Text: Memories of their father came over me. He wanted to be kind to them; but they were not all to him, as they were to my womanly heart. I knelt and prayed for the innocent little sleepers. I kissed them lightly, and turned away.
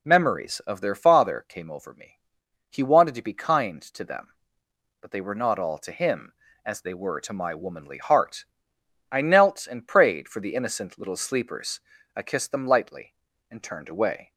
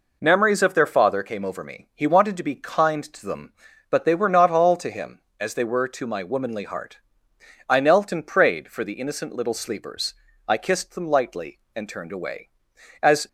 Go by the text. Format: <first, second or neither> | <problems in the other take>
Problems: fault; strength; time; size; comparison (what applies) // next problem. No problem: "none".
first | goes on to say "As"; slight; from 13.0 s on; 0.26 s long